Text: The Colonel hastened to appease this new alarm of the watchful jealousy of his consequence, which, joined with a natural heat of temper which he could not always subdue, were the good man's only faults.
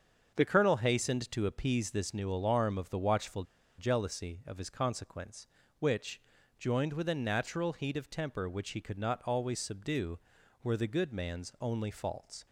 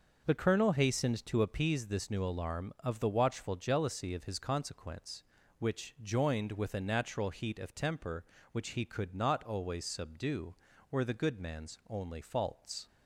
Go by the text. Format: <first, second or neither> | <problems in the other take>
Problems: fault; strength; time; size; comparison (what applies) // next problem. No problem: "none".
second | starts louder than the rest; until 1.3 s; 7 dB // pauses between "watchful" and "jealousy"; slight; at 3.4 s; 0.35 s long